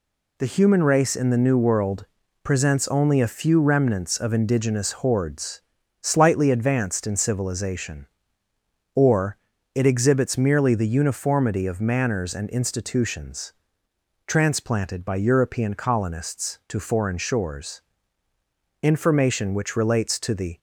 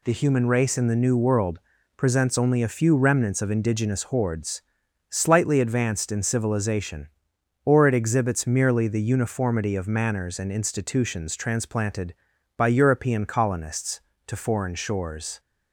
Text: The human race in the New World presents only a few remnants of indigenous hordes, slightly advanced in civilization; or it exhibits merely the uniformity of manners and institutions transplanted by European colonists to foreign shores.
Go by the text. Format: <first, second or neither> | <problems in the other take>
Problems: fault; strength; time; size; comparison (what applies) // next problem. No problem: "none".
second | pauses between "World" and "presents"; slight; at 2.0 s; 0.36 s long; slight in the second // pauses between "or" and "it"; at 9.3 s; 0.40 s long // pauses between "institutions" and "transplanted"; noticeable; at 13.5 s; 0.74 s long // goes on to say "Information which relates to the"; strong; from 18.8 s on; 1.7 s long